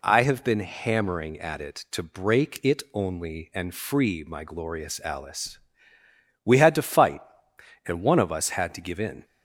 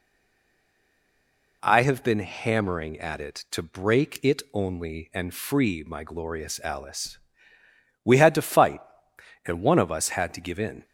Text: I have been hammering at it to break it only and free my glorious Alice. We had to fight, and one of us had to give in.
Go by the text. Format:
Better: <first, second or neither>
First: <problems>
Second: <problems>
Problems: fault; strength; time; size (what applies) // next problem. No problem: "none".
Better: first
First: none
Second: stays silent before the first word; noticeable; until 1.6 s; 1.6 s long